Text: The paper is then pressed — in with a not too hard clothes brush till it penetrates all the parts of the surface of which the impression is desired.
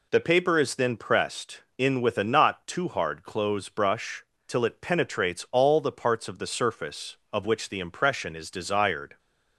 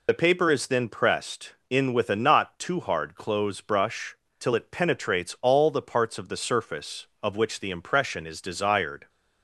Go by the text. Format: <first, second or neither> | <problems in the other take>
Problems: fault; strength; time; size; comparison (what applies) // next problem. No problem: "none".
first | loses the start of "The"; at 0.0 s; 50 ms // pauses between "brush" and "till"; slight; at 4.1 s; 0.22 s long; slight in the first